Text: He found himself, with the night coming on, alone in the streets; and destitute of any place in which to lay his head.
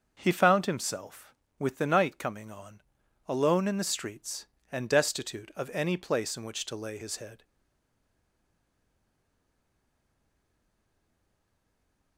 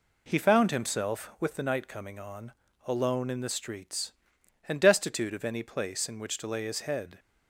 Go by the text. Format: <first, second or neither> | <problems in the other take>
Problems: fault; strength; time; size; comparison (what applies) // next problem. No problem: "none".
second | starts louder than the rest; until 1.2 s; 6.5 dB // stays silent after the last word; strong; from 7.4 s on; 4.7 s long